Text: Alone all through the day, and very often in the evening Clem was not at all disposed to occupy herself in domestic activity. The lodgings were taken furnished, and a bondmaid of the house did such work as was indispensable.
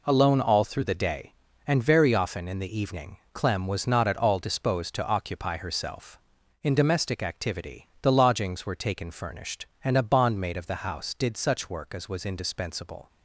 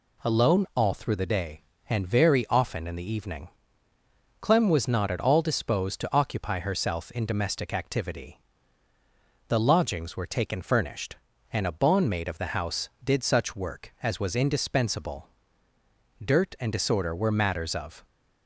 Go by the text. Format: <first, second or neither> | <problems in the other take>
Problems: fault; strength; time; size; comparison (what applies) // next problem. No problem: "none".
first | pauses between "evening" and "Clem"; noticeable; at 3.4 s; 0.92 s long; slight in the first // goes on to say "Dirt and disorder were matters of"; strong; from 16.2 s on; 1.8 s long